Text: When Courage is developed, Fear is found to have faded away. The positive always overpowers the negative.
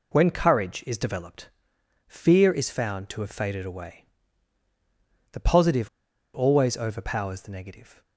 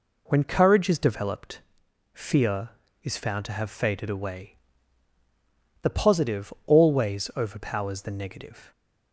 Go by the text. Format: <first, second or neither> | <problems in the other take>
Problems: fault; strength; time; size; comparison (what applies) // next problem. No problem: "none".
second | pauses between "positive" and "always"; at 5.8 s; 0.45 s long